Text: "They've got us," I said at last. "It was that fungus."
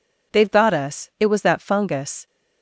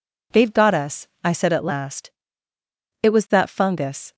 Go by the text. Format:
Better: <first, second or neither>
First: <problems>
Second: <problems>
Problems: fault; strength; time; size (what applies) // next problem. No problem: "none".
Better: second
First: skips "I said at last"; at 1.1 s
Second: none